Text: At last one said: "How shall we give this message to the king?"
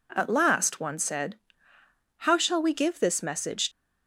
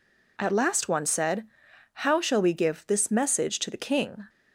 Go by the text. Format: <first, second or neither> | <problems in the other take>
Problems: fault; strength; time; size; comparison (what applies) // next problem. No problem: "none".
second | stops before "to the king"; at 3.7 s